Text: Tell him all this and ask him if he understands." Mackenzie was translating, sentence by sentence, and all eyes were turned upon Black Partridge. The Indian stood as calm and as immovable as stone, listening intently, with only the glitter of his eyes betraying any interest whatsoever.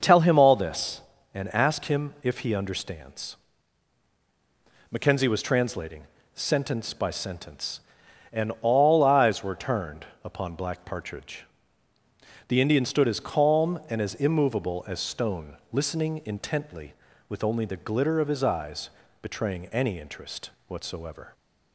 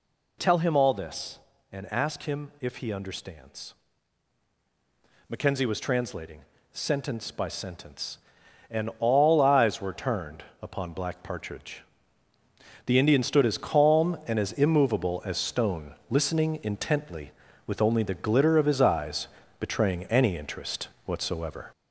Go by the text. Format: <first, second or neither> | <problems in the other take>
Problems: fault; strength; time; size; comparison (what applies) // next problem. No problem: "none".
first | gets louder; noticeable; throughout; 4 dB // pauses between "turned" and "upon"; slight; at 10.4 s; 0.18 s long; slight in the first // pauses between "eyes" and "betraying"; slight; at 19.2 s; 0.32 s long; slight in the first // pauses between "interest" and "whatsoever"; slight; at 20.8 s; 0.18 s long; slight in the first